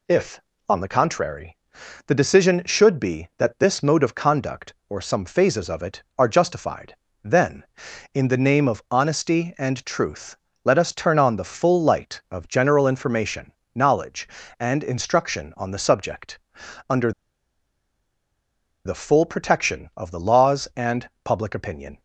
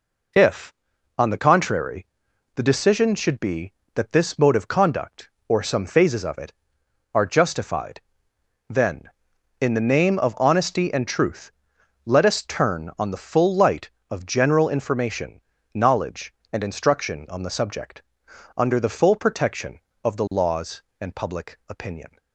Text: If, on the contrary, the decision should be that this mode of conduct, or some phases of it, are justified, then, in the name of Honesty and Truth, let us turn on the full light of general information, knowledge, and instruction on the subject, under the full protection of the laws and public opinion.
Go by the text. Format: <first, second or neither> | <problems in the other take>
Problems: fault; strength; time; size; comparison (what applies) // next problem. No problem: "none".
second | pauses between "under" and "the"; strong; at 17.1 s; 1.7 s long // pauses between "and" and "public"; slight; at 21.0 s; 0.16 s long